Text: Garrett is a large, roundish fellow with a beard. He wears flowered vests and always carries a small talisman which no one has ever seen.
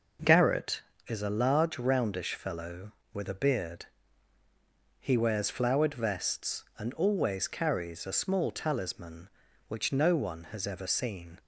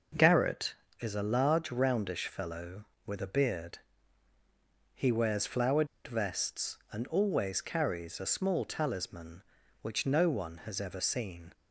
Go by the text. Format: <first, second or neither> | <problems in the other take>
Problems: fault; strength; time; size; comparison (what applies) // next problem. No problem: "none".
first | pauses between "flowered" and "vests"; slight; at 5.8 s; 0.19 s long